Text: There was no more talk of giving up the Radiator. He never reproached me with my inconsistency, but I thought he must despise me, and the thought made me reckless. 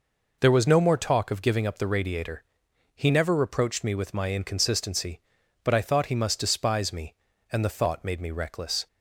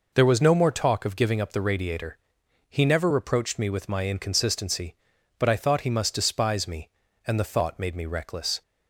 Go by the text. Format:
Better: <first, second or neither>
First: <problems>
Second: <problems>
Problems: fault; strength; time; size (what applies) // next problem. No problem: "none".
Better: neither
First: none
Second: none